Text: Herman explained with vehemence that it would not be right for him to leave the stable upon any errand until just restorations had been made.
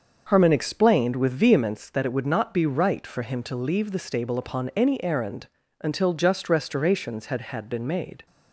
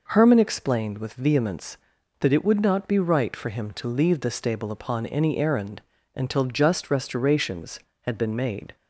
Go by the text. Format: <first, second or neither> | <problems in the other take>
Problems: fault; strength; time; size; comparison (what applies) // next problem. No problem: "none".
second | starts louder than the rest; until 1.2 s; 6.5 dB // pauses between "errand" and "until"; slight; at 5.4 s; 0.32 s long; slight in the second // says "had" twice; at 7.3 s